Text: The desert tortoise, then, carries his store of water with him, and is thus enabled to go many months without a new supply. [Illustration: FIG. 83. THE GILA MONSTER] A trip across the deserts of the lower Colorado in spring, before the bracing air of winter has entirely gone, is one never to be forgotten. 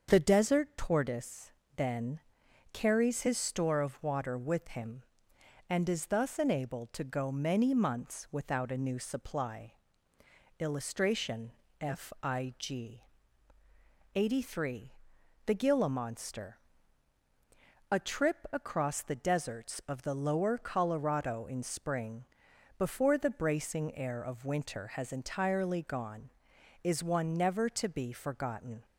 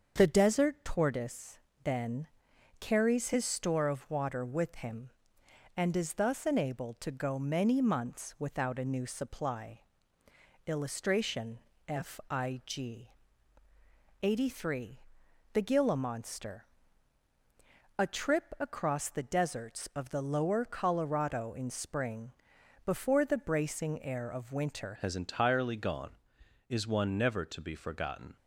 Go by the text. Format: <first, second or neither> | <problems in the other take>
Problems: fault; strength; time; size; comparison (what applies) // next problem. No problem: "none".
first | starts louder than the rest; until 1.1 s; 7 dB; also in the first // pauses between "MONSTER" and "A"; strong; at 16.6 s; 1.3 s long; strong in the first // changes voice at "has"; from 24.9 s on; 3.4 s long